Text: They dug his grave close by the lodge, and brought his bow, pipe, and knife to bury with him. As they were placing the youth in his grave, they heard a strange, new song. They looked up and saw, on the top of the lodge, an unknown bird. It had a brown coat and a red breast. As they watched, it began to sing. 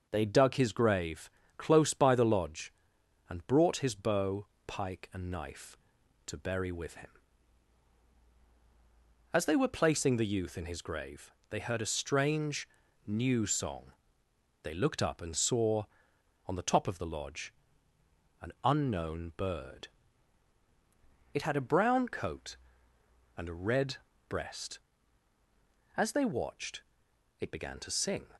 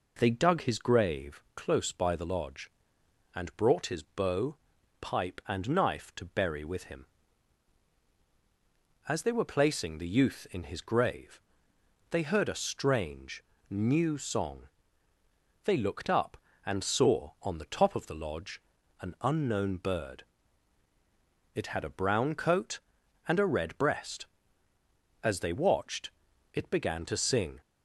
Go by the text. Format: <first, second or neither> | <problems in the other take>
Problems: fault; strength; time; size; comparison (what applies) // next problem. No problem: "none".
second | pauses between "grave" and "close"; slight; at 1.2 s; 0.28 s long // says "pike" for "pipe"; at 4.6 s // pauses between "red" and "breast"; slight; at 23.9 s; 0.32 s long